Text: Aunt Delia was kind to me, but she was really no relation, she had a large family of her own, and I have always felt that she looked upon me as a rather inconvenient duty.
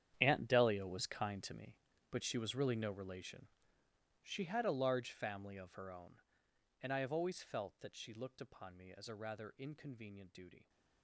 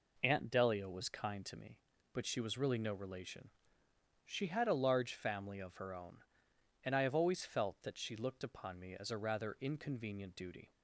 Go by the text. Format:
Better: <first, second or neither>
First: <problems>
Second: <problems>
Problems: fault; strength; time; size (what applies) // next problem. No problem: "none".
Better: second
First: gets quieter; strong; throughout; 16 dB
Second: none